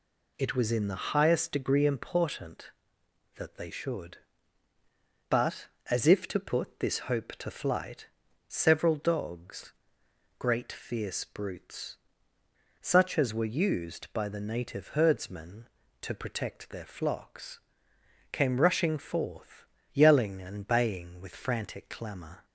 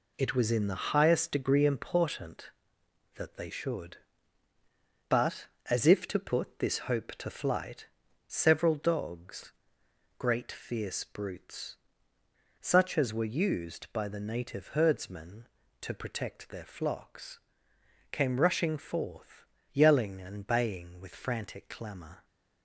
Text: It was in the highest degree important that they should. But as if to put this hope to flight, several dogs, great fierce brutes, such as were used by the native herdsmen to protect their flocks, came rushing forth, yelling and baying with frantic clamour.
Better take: first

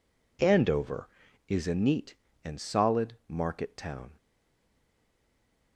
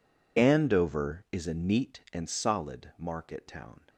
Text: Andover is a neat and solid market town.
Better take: second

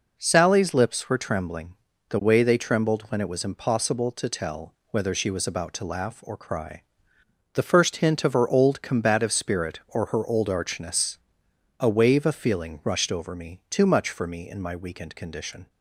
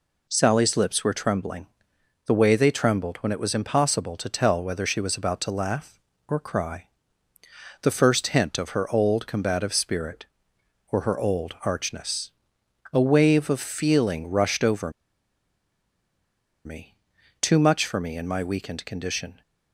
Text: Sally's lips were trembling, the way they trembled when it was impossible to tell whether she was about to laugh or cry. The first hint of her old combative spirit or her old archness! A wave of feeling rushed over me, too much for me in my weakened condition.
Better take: first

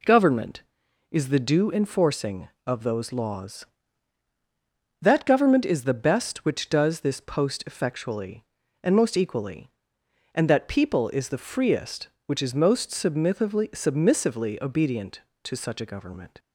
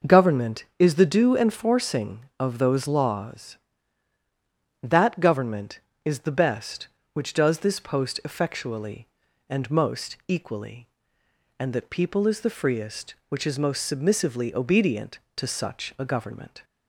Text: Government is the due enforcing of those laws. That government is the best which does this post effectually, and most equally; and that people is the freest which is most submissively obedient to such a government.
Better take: second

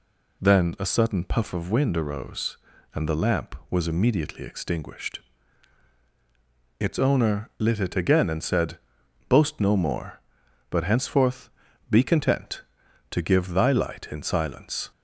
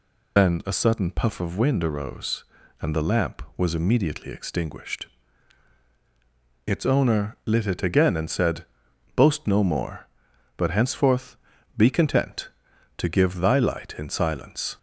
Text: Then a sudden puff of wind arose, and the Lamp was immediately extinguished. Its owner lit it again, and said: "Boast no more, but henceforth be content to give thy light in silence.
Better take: first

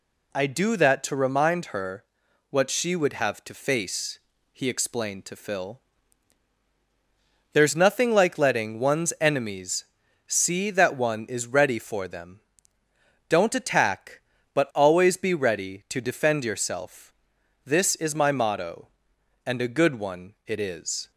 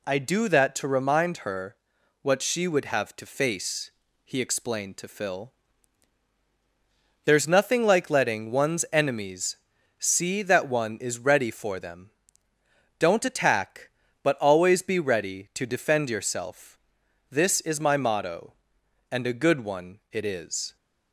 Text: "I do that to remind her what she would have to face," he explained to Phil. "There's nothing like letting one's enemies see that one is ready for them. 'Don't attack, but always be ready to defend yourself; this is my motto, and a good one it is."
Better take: neither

